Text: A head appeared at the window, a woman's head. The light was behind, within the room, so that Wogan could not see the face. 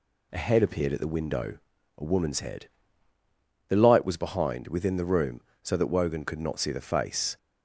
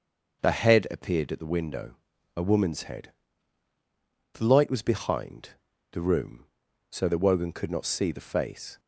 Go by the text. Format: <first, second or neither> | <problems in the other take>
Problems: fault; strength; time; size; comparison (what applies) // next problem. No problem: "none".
first | skips "within"; at 5.7 s